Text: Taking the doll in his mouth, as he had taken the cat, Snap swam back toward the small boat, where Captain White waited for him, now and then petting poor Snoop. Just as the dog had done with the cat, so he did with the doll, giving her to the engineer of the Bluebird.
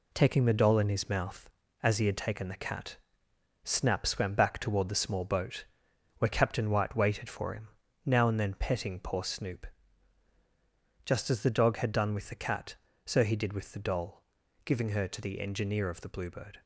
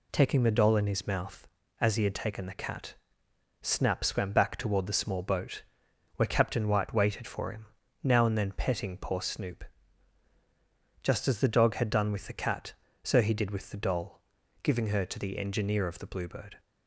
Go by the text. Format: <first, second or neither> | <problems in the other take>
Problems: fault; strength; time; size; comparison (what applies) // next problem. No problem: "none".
second | gets quieter; throughout; 6.5 dB